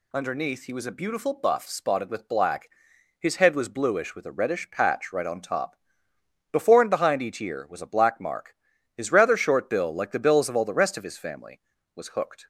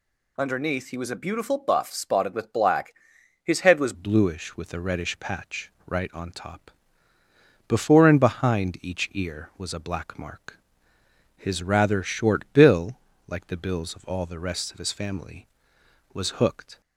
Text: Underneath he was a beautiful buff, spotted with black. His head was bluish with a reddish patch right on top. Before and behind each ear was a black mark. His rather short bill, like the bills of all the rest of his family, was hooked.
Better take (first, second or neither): first